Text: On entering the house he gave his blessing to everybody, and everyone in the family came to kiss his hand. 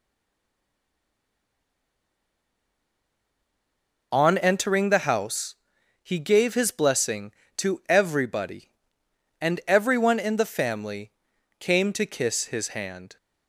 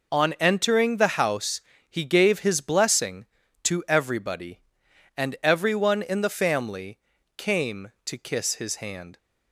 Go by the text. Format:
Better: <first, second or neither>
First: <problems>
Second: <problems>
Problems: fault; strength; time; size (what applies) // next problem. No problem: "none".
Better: second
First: stays silent before the first word; strong; until 4.1 s; 4.1 s long // pauses between "house" and "he"; noticeable; at 5.5 s; 0.48 s long // pauses between "family" and "came"; noticeable; at 11.1 s; 0.48 s long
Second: pauses between "house" and "he"; slight; at 1.6 s; 0.28 s long // pauses between "family" and "came"; at 6.9 s; 0.38 s long